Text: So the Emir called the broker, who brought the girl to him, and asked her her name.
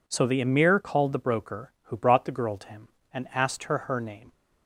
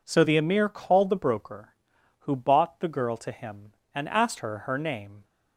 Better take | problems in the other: first | says "bought" for "brought"; at 2.3 s

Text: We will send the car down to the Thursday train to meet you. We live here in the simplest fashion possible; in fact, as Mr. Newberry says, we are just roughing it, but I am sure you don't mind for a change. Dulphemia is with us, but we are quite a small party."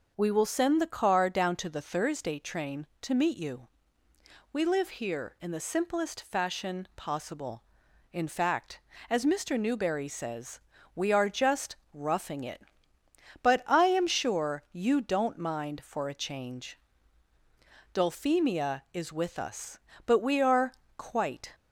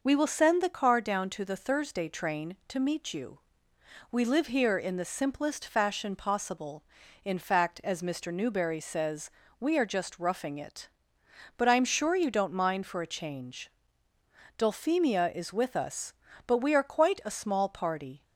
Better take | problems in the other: second | pauses between "just" and "roughing"; slight; at 11.7 s; 0.18 s long // pauses between "are" and "quite"; slight; at 20.7 s; 0.24 s long // stops before "a small party"; at 21.5 s

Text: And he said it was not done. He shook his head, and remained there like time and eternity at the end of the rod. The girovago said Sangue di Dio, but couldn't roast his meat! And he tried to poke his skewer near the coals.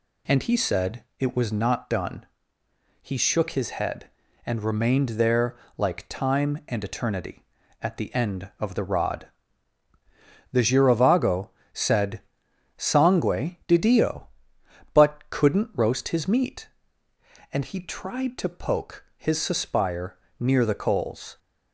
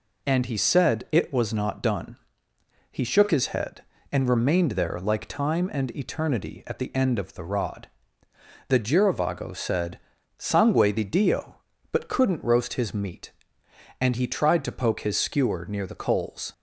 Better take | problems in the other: second | pauses between "there" and "like"; slight; at 5.5 s; 0.20 s long // pauses between "girovago" and "said"; slight; at 11.5 s; 0.22 s long // pauses between "said" and "Sangue"; noticeable; at 12.2 s; 0.56 s long; also in the second // says "suspire" for "skewer"; at 19.4 s

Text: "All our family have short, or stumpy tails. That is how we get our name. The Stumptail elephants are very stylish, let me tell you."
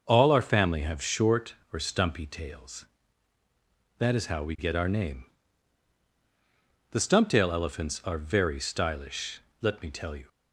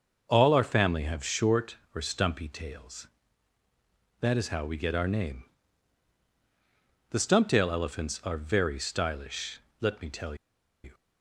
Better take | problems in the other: first | starts louder than the rest; noticeable; until 1.3 s; 6 dB // pauses between "tell" and "you"; noticeable; at 10.3 s; 0.48 s long

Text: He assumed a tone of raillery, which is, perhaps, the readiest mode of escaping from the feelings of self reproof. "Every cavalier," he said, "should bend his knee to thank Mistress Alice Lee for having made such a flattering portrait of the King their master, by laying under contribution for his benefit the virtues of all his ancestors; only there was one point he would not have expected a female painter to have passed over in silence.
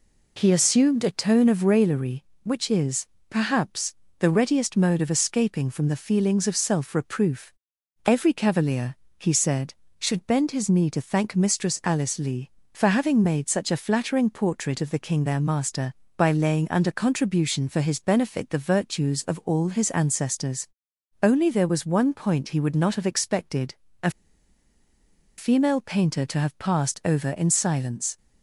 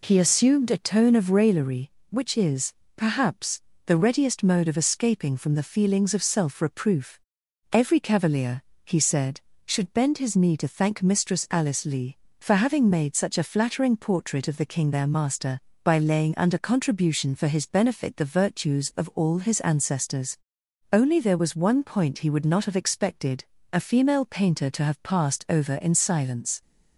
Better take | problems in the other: second | pauses between "expected" and "a"; slight; at 23.7 s; 0.30 s long; slight in the second // pauses between "a" and "female"; strong; at 24.1 s; 1.2 s long

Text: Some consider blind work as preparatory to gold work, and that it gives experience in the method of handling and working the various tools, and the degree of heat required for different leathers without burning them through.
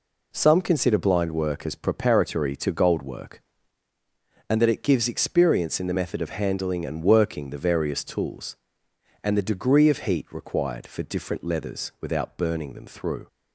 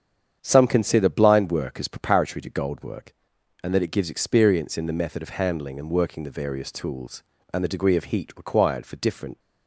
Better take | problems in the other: first | starts louder than the rest; strong; until 1.4 s; 8 dB // stops before "leathers without burning them through"; at 9.3 s

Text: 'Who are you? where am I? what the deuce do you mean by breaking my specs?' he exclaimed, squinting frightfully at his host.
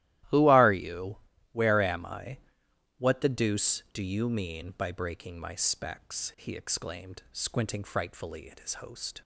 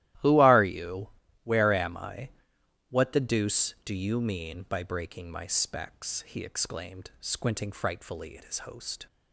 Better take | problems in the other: neither | starts louder than the rest; strong; the same in both

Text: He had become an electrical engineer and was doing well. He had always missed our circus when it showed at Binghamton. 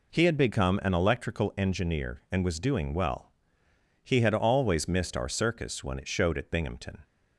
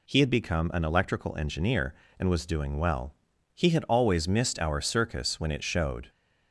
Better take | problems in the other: first | stops before "at Binghamton"; at 6.0 s

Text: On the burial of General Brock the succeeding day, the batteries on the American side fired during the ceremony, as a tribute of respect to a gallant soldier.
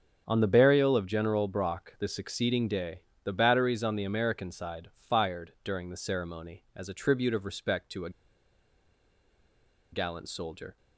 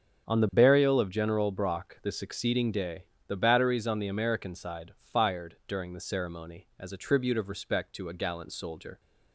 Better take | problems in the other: second | starts louder than the rest; strong; until 1.2 s; 7.5 dB; strong in the second // pauses between "a" and "gallant"; strong; at 8.1 s; 1.8 s long

